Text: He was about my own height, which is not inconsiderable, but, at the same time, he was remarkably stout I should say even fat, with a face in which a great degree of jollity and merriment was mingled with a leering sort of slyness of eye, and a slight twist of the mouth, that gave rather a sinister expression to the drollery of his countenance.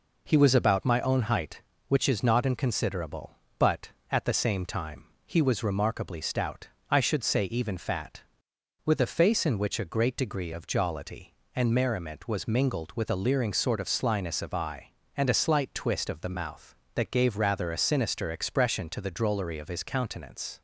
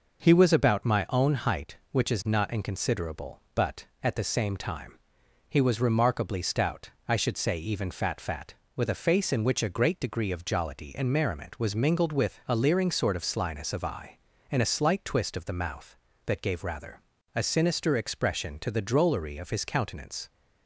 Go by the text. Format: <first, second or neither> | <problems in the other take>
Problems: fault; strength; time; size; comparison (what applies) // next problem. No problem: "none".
first | pauses between "stout" and "I"; slight; at 6.8 s; 0.16 s long; slight in the first // says "fat" twice; at 8.2 s // pauses between "rather" and "a"; slight; at 17.0 s; 0.34 s long